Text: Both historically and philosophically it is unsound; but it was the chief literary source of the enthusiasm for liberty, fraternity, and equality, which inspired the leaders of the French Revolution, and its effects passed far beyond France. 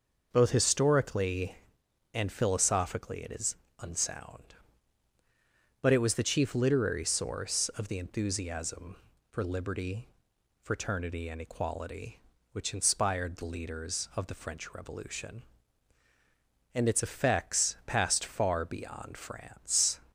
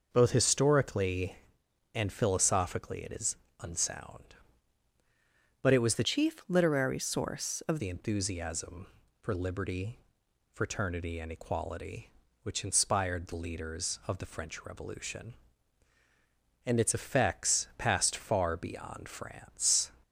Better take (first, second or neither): first